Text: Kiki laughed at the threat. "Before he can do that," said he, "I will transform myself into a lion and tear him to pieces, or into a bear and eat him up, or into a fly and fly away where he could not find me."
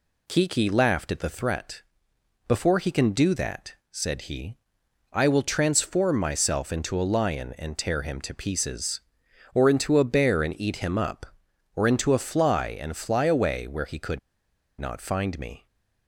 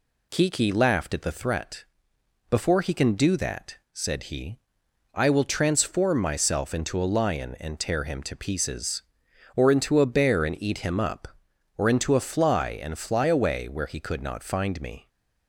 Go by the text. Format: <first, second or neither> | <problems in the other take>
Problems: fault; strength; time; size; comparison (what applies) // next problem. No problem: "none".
second | pauses between "could" and "not"; noticeable; at 14.1 s; 0.60 s long